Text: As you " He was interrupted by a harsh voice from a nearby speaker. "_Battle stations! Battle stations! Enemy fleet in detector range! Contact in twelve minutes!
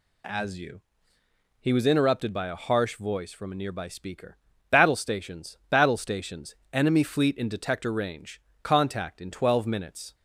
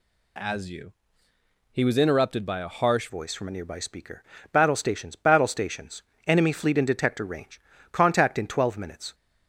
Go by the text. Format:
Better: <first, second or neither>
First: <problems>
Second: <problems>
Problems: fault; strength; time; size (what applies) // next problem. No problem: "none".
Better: first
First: none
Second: changes voice at "voice"; from 3.0 s on; 6.1 s long